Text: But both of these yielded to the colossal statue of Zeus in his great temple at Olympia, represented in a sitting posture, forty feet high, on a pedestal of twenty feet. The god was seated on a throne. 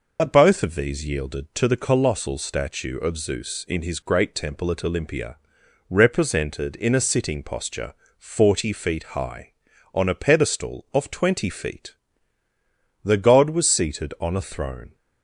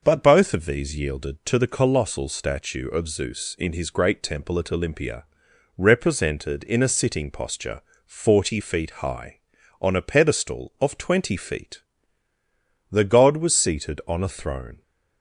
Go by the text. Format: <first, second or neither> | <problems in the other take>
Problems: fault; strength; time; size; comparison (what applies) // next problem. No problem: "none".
second | loses the start of "But"; at 0.1 s; 60 ms